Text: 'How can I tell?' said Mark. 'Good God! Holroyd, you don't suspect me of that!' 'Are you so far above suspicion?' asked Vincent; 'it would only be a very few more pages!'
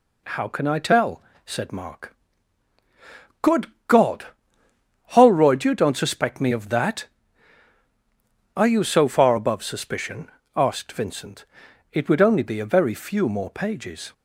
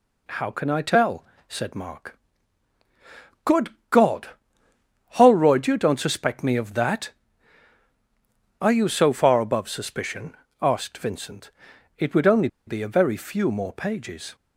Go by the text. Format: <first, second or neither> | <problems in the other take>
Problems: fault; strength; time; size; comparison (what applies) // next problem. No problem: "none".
first | pauses between "Good" and "God"; slight; at 3.7 s; 0.20 s long; slight in the first // pauses between "only" and "be"; slight; at 12.4 s; 0.18 s long